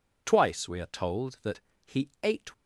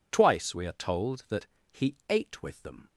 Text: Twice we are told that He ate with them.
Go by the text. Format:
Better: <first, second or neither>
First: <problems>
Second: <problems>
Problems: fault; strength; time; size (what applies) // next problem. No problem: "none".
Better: second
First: pauses between "that" and "He"; slight; at 1.6 s; 0.22 s long // stops before "with them"; at 2.5 s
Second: pauses between "that" and "He"; slight; at 1.4 s; 0.22 s long